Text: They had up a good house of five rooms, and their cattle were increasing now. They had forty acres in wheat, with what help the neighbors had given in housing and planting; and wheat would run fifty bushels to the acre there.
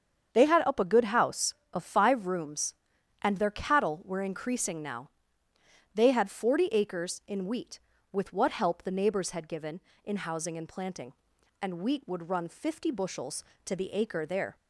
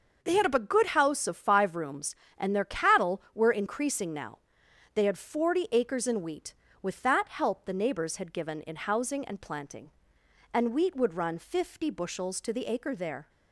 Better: first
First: starts louder than the rest; strong; until 1.3 s; 7.5 dB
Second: starts louder than the rest; noticeable; until 1.2 s; 6 dB // says "that" for "what"; at 7.0 s

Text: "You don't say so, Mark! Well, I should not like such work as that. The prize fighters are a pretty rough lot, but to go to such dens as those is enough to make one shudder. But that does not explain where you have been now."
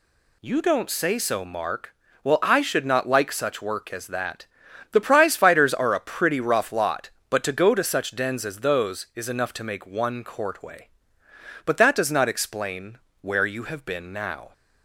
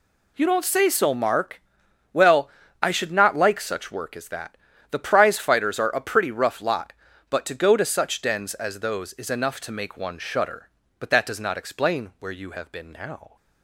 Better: second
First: says "courtway" for "shudder"; at 10.2 s // pauses between "explain" and "where"; slight; at 12.9 s; 0.24 s long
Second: none

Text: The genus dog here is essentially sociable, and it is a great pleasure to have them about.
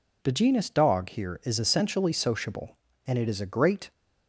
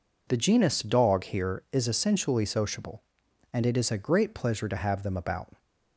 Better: second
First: stops before "pleasure to have them about"; at 3.9 s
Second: none

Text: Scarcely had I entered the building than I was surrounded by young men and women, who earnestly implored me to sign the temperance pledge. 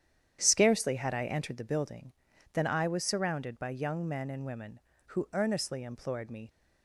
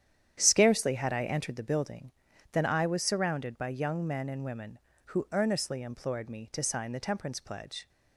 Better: second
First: starts louder than the rest; strong; until 1.4 s; 9.5 dB // stops before "to sign the temperance pledge"; at 6.4 s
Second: starts louder than the rest; strong; until 1.4 s; 9.5 dB

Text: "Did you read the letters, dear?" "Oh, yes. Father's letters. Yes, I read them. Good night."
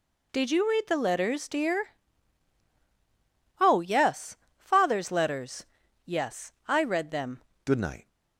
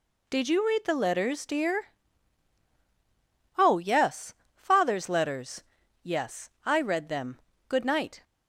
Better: second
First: changes voice at "Good"; from 7.6 s on; 0.4 s long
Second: none

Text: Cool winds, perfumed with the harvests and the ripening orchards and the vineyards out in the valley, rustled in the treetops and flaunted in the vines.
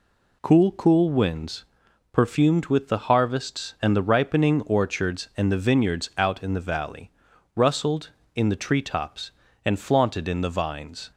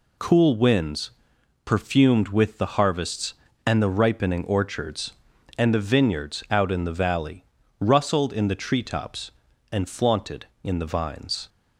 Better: second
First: says "Cool" twice; at 0.7 s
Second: none

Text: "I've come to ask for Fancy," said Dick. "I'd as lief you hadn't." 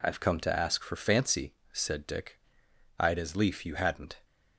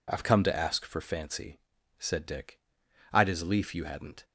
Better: neither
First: none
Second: none

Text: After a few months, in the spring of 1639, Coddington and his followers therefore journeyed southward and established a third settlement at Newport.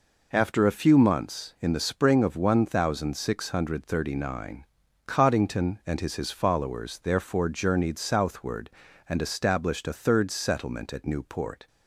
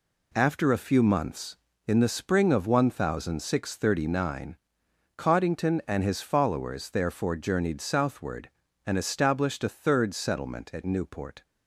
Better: second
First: says "his" twice; at 6.1 s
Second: none

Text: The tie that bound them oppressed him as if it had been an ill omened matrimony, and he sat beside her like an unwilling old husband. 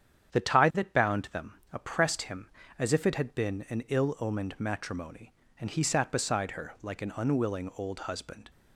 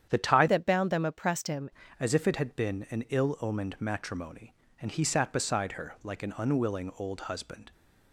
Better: first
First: starts louder than the rest; strong; until 1.3 s; 8.5 dB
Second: starts louder than the rest; strong; until 1.1 s; 9 dB // changes voice from "that" to "him"; from 0.4 to 1.6 s; 1.2 s long

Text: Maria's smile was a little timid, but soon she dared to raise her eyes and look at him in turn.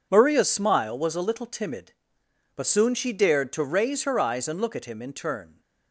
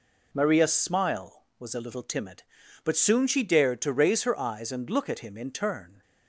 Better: neither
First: none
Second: none

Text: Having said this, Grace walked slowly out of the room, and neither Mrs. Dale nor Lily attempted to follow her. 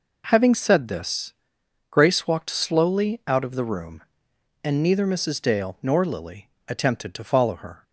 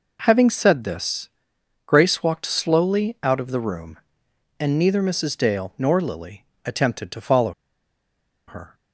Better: first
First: pauses between "Lily" and "attempted"; slight; at 6.4 s; 0.16 s long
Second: pauses between "Lily" and "attempted"; slight; at 6.4 s; 0.18 s long // pauses between "follow" and "her"; noticeable; at 7.5 s; 0.95 s long

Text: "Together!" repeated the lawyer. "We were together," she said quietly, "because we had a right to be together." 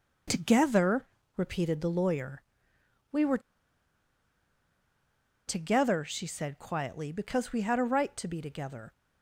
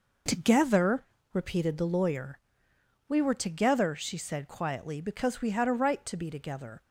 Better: second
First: pauses between "were" and "together"; strong; at 3.3 s; 2.0 s long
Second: none

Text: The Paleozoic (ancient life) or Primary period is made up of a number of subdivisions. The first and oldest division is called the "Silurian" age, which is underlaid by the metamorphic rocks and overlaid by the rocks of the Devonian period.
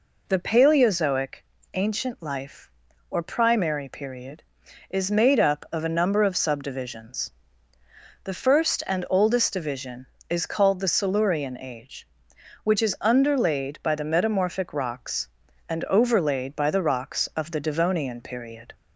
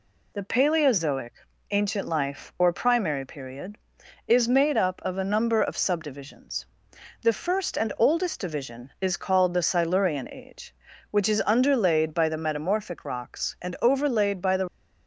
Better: first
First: none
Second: stops before "rocks of the Devonian period"; at 14.6 s

